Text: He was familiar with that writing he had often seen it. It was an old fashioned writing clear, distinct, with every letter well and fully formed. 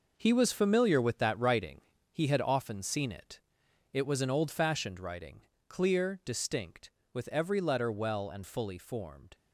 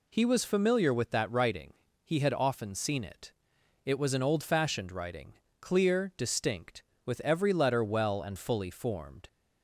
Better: second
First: gets quieter; strong; throughout; 9 dB // pauses between "writing" and "he"; slight; at 1.8 s; 0.30 s long // pauses between "writing" and "clear"; slight; at 5.4 s; 0.26 s long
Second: pauses between "writing" and "he"; slight; at 1.7 s; 0.30 s long // pauses between "writing" and "clear"; slight; at 5.3 s; 0.26 s long

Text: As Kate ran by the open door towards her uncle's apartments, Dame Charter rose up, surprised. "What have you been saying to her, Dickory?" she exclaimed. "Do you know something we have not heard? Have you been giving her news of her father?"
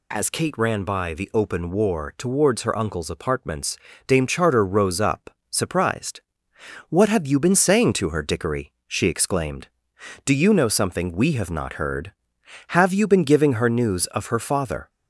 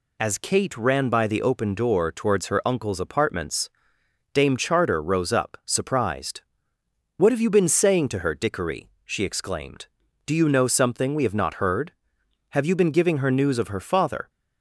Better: second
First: says "war" for "door"; at 1.7 s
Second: none

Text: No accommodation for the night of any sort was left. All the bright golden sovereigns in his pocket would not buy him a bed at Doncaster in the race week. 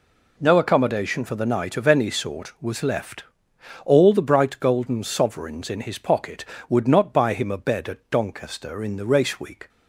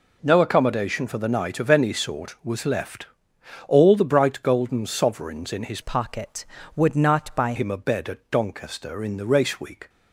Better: first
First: none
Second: changes voice from "pocket" to "buy"; from 5.8 to 7.5 s; 1.7 s long

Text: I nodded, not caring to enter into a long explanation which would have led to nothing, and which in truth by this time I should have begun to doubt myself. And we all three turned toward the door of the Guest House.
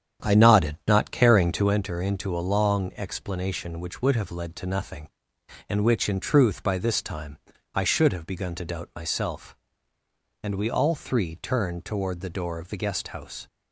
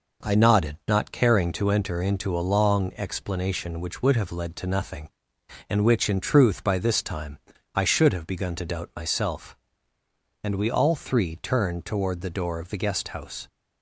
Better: second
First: starts louder than the rest; strong; until 1.7 s; 9 dB // pauses between "time" and "I"; slight; at 7.3 s; 0.34 s long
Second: pauses between "time" and "I"; slight; at 7.3 s; 0.34 s long

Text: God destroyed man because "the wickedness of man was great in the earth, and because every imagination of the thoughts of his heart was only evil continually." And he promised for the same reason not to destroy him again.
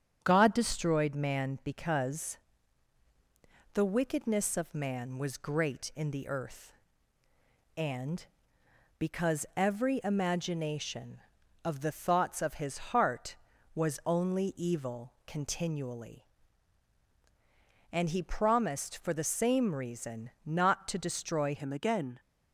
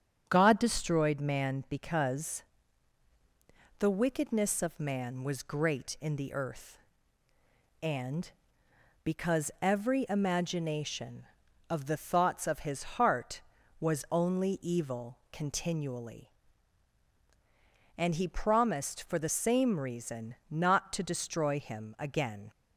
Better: second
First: starts louder than the rest; strong; until 1.2 s; 8.5 dB // pauses between "because" and "the"; strong; at 2.3 s; 1.3 s long // pauses between "reason" and "not"; slight; at 20.2 s; 0.16 s long // changes voice at "him"; from 21.5 s on; 0.6 s long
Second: starts louder than the rest; strong; until 1.2 s; 8.5 dB // pauses between "because" and "the"; strong; at 2.4 s; 1.3 s long // pauses between "reason" and "not"; slight; at 20.3 s; 0.16 s long

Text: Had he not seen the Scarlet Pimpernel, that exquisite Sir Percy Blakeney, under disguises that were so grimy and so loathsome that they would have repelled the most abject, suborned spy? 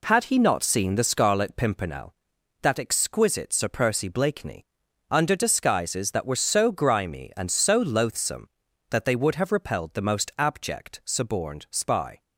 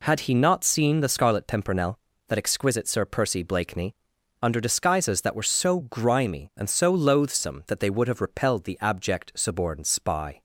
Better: first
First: none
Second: skips "most"; at 8.8 s

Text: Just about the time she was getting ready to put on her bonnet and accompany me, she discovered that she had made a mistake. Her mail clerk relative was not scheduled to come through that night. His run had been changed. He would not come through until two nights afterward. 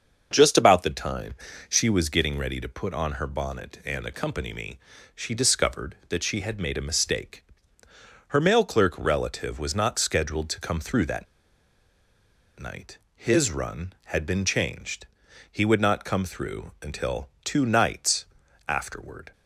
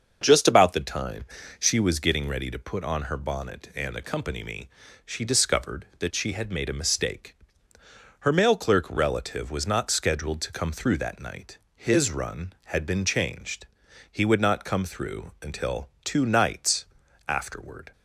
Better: second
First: starts louder than the rest; until 1.3 s; 6.5 dB // pauses between "time" and "she"; slight; at 1.3 s; 0.34 s long // pauses between "that" and "night"; strong; at 11.2 s; 1.3 s long // pauses between "until" and "two"; slight; at 17.2 s; 0.16 s long // pauses between "nights" and "afterward"; at 18.2 s; 0.42 s long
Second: starts louder than the rest; until 1.2 s; 6.5 dB // pauses between "time" and "she"; slight; at 1.2 s; 0.34 s long // pauses between "until" and "two"; slight; at 15.8 s; 0.16 s long // pauses between "nights" and "afterward"; at 16.8 s; 0.42 s long

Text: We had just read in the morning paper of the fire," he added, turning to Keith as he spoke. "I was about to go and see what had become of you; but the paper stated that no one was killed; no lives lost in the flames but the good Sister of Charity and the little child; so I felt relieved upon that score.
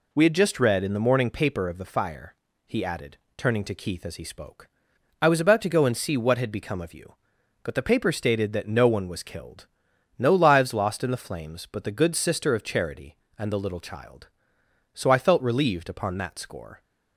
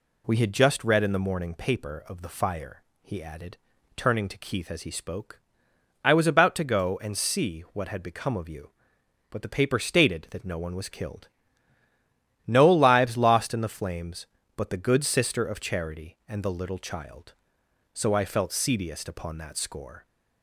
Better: first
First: none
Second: says "seediest" for "relieved"; at 18.5 s

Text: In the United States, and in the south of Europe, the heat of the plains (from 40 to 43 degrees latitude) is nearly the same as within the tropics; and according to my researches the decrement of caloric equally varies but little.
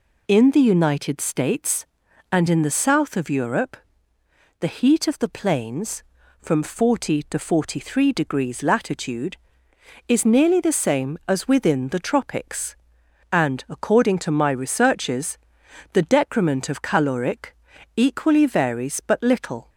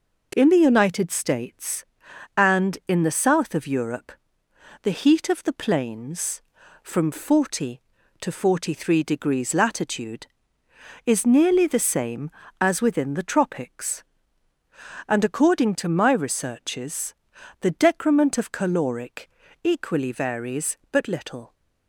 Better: neither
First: pauses between "researches" and "the"; noticeable; at 15.3 s; 0.54 s long // pauses between "caloric" and "equally"; at 17.5 s; 0.40 s long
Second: pauses between "researches" and "the"; noticeable; at 17.1 s; 0.48 s long // pauses between "caloric" and "equally"; slight; at 19.2 s; 0.34 s long

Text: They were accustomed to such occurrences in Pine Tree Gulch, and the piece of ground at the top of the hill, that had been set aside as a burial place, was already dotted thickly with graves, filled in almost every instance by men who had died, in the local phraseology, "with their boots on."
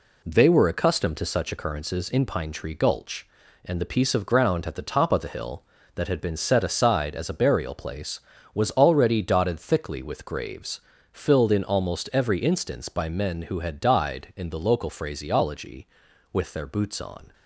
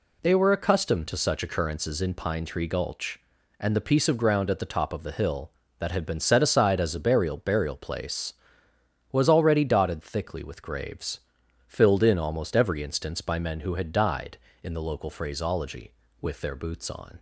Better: first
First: none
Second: says "burial" twice; at 7.3 s

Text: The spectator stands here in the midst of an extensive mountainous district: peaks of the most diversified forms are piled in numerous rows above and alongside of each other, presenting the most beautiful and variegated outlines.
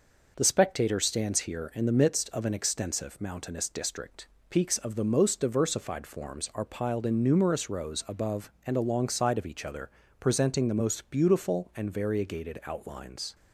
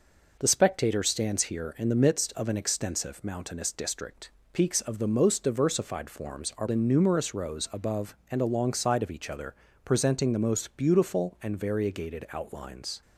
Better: first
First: none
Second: skips "piled"; at 6.6 s

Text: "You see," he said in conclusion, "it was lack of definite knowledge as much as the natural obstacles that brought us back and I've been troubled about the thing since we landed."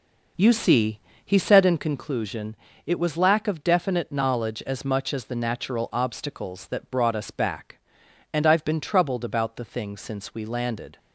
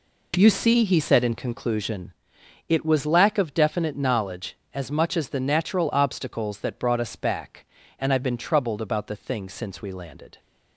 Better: second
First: starts louder than the rest; noticeable; until 1.9 s; 5 dB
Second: none

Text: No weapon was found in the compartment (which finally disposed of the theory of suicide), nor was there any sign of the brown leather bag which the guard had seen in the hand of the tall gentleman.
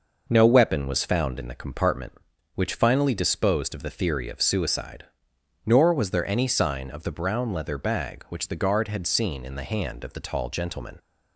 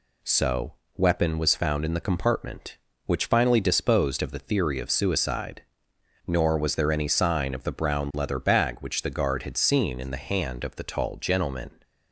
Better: first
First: none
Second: says "So" for "No"; at 0.2 s

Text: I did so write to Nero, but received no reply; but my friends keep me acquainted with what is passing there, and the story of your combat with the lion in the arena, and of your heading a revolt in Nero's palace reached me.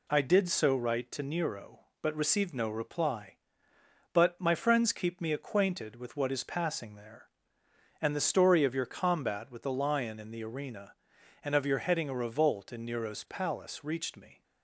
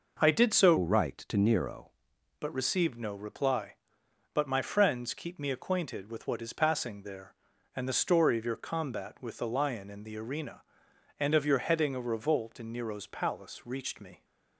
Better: first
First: none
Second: changes voice from "write" to "Nero"; from 0.7 to 1.8 s; 1.1 s long

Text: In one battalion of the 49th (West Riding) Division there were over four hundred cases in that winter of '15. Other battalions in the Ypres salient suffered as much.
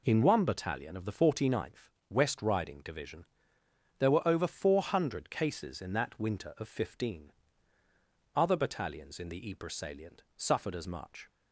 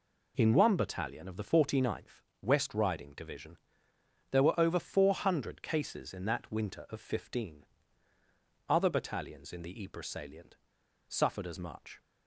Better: first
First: pauses between "Division" and "there"; noticeable; at 3.2 s; 0.76 s long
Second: pauses between "Division" and "there"; noticeable; at 3.5 s; 0.76 s long // pauses between "salient" and "suffered"; noticeable; at 10.5 s; 0.51 s long

